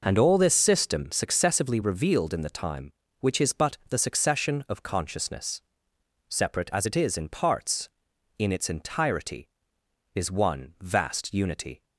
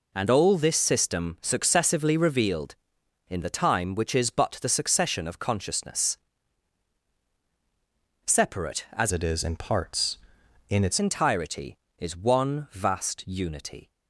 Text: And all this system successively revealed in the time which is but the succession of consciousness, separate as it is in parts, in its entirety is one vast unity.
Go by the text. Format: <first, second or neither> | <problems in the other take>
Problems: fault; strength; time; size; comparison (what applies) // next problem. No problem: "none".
first | changes voice from "it" to "its"; from 9.1 to 10.9 s; 1.8 s long